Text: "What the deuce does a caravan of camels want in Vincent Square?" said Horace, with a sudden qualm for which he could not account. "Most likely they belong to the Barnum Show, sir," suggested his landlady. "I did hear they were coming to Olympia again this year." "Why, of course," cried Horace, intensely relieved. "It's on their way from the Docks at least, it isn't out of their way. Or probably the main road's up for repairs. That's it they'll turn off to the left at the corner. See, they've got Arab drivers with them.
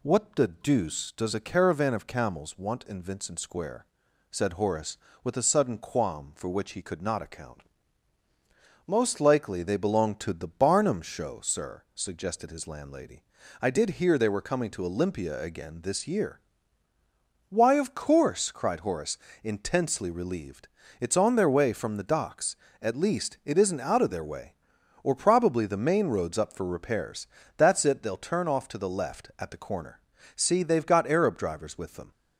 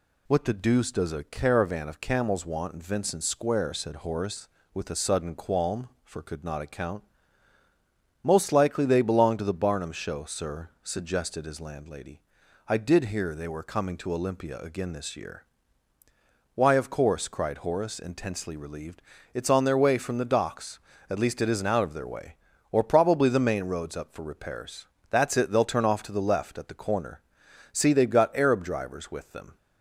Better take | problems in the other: first | skips "which he"; at 6.2 s

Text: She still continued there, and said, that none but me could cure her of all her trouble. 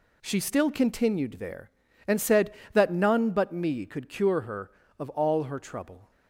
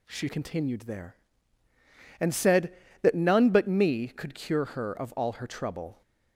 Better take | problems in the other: first | skips "still"; at 0.2 s

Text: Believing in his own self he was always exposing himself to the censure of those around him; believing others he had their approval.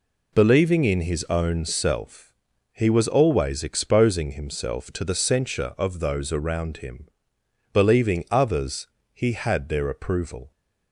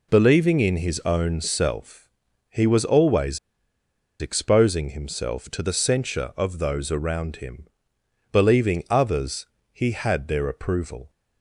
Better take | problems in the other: first | pauses between "self" and "he"; at 2.0 s; 0.40 s long; also in the first // pauses between "always" and "exposing"; noticeable; at 3.3 s; 0.83 s long // pauses between "others" and "he"; slight; at 9.4 s; 0.26 s long; slight in the first

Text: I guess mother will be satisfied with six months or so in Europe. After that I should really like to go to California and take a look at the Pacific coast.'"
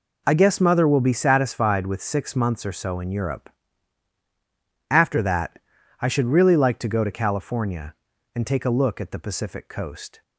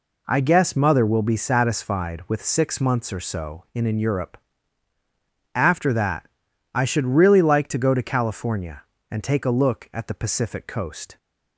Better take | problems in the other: first | says "in" twice; at 3.8 s // pauses between "that" and "I"; noticeable; at 6.2 s; 0.46 s long; also in the first

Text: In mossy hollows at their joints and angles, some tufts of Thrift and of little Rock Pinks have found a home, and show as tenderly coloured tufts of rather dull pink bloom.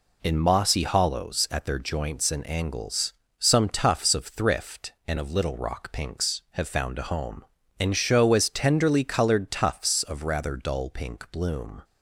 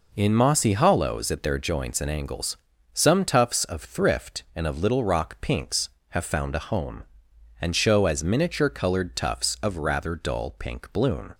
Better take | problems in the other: first | says "miniature" for "tenderly"; at 8.2 s

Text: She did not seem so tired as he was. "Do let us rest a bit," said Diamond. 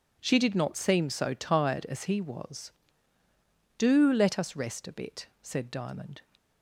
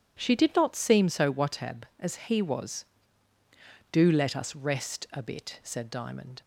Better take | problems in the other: first | says "watab" for "tired"; at 1.3 s

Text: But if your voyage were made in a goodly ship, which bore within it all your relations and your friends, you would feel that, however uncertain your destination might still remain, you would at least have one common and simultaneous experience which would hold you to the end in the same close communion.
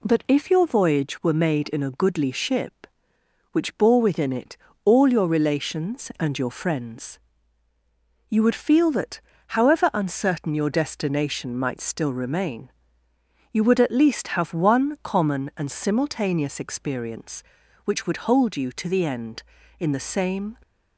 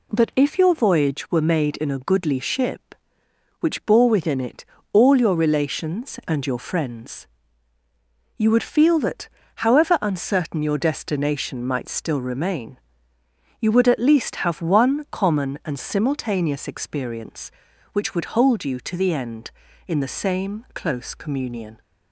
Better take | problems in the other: second | pauses between "it" and "all"; slight; at 4.5 s; 0.28 s long; slight in the second // stops before "close communion"; at 20.6 s

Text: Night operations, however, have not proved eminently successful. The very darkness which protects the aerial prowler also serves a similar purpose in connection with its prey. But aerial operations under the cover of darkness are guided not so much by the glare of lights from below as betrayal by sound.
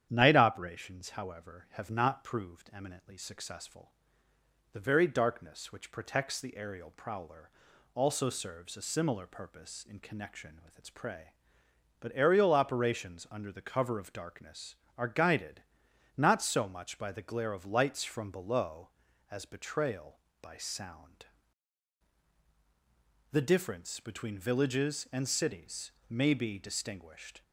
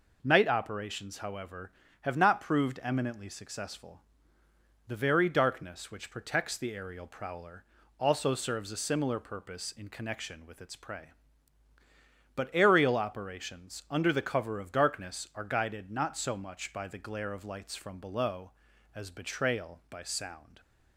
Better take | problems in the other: second | starts louder than the rest; strong; until 1.1 s; 9.5 dB // pauses between "prowler" and "also"; at 7.5 s; 0.44 s long; slight in the second // pauses between "guided" and "not"; noticeable; at 15.6 s; 0.56 s long // goes on to say "The difference between villages and cities may be distinguished"; strong; from 23.3 s on; 4.1 s long

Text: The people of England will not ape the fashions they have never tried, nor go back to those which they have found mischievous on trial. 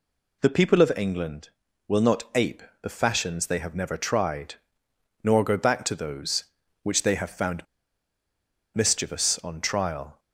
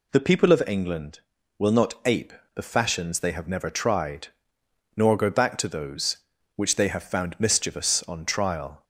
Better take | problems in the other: second | pauses between "ape" and "the"; slight; at 2.6 s; 0.20 s long; slight in the second // pauses between "found" and "mischievous"; at 7.6 s; 1.1 s long

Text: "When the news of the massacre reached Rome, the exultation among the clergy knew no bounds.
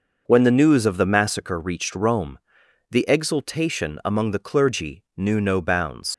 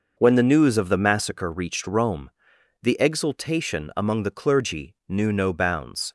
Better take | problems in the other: second | leaves "bounds" unfinished; at 6.1 s; 55 ms

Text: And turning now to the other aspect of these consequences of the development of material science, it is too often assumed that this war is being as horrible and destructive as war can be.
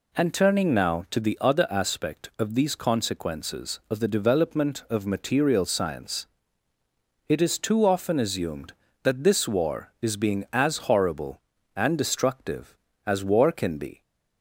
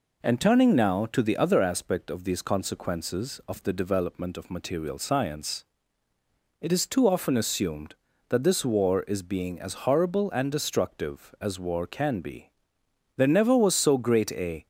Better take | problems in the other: first | goes on to say "There never was so great a"; from 13.1 s on; 1.5 s long

